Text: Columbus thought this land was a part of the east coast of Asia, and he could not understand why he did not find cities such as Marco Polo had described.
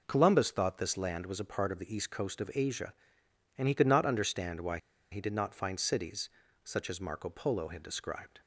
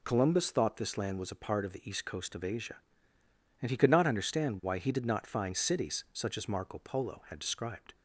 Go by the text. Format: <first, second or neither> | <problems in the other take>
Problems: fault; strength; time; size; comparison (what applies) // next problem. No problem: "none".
second | pauses between "why" and "he"; slight; at 4.7 s; 0.34 s long // pauses between "cities" and "such"; slight; at 6.2 s; 0.34 s long